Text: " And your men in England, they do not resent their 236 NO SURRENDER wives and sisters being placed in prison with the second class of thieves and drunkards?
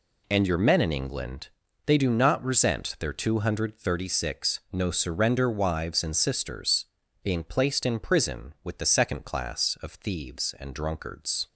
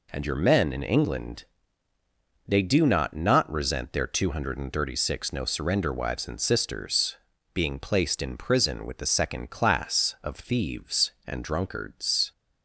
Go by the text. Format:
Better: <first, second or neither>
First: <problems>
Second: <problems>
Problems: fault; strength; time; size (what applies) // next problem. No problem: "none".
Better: first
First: pauses between "sisters" and "being"; at 6.8 s; 0.38 s long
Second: says "not" twice; at 3.1 s // pauses between "sisters" and "being"; at 7.1 s; 0.38 s long